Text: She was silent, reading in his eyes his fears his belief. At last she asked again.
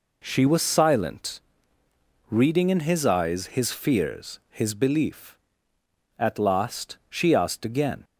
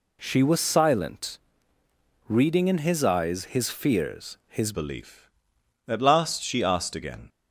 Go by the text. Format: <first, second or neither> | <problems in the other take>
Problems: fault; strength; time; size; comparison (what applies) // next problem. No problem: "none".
first | changes voice at "belief"; from 4.7 s on; 2.5 s long